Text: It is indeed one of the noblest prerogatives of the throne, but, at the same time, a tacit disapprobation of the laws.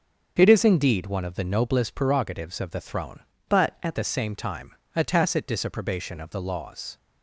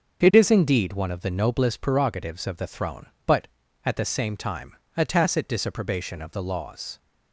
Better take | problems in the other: second | starts louder than the rest; until 1.3 s; 6.5 dB // changes voice from "but" to "at"; from 3.4 to 3.9 s; 0.5 s long

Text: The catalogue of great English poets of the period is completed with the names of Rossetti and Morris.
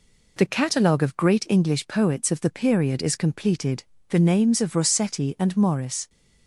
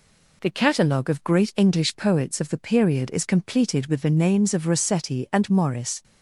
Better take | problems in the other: second | skips "with"; at 3.9 s

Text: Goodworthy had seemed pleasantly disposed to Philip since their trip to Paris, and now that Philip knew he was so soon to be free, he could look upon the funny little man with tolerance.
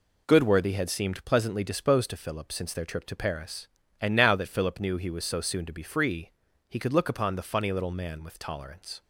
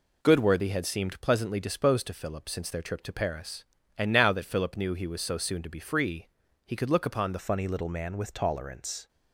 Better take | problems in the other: first | changes voice at "funny"; from 7.3 s on; 1.7 s long

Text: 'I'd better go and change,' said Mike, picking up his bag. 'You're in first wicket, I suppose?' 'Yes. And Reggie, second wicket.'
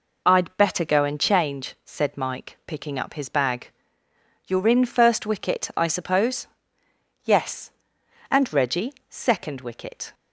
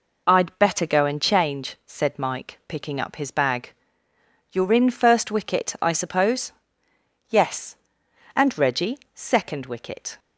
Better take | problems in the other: neither | none

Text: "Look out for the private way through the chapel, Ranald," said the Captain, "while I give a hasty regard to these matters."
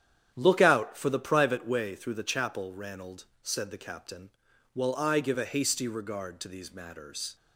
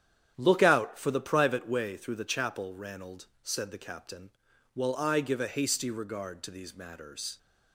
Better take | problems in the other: neither | starts louder than the rest; strong; the same in both

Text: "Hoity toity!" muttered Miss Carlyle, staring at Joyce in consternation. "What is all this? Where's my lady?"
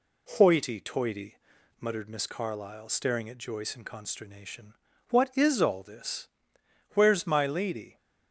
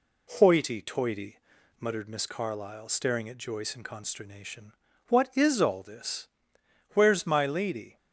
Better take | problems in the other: neither | none

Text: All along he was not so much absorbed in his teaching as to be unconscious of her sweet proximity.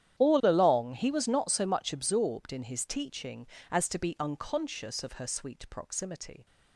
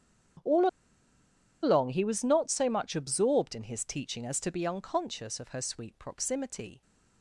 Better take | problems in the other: first | starts louder than the rest; strong; until 2.3 s; 9.5 dB; strong in the first // pauses between "All" and "along"; noticeable; at 0.6 s; 0.94 s long

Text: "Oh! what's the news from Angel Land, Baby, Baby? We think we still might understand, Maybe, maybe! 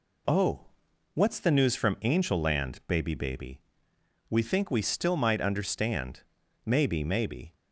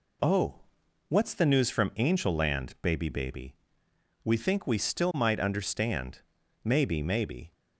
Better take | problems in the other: neither | none

